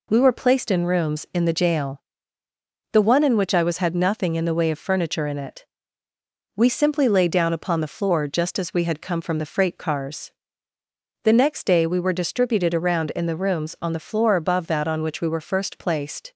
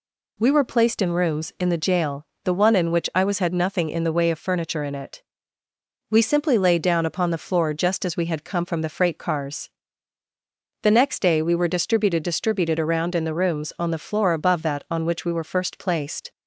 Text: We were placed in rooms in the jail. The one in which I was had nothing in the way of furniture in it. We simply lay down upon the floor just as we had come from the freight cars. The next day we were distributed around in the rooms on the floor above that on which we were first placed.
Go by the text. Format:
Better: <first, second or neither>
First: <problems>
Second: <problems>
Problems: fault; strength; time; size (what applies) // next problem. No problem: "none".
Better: first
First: none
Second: says "distributed" twice; at 12.2 s